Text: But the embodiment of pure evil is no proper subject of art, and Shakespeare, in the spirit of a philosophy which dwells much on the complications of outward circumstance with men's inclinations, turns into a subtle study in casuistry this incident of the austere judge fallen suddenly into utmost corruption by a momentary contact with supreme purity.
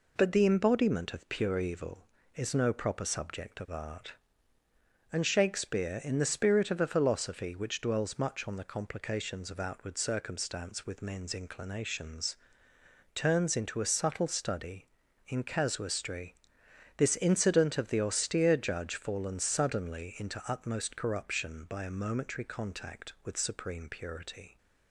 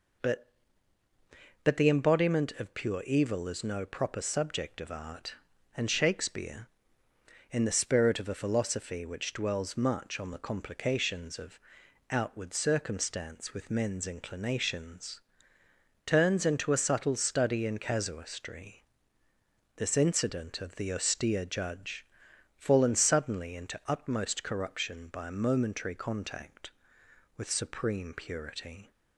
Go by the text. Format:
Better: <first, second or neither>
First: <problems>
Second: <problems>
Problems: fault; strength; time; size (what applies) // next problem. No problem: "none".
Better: first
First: pauses between "casuistry" and "this"; noticeable; at 16.3 s; 0.62 s long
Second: says "But" twice; at 1.6 s // pauses between "of" and "outward"; noticeable; at 11.5 s; 0.52 s long // pauses between "casuistry" and "this"; noticeable; at 18.8 s; 0.94 s long // pauses between "judge" and "fallen"; noticeable; at 22.0 s; 0.52 s long